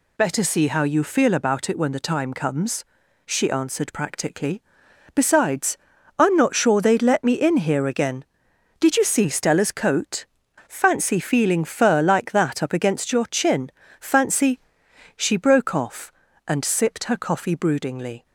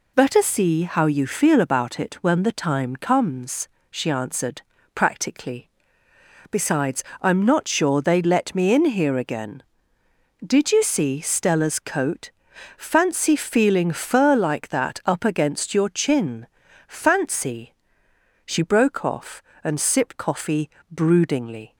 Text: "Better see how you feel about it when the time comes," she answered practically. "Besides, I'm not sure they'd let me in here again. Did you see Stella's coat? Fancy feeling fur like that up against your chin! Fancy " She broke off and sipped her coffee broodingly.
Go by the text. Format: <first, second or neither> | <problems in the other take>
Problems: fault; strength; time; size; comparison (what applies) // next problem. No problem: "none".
first | pauses between "answered" and "practically"; slight; at 4.6 s; 0.34 s long // skips "her"; at 20.1 s // pauses between "coffee" and "broodingly"; slight; at 20.6 s; 0.20 s long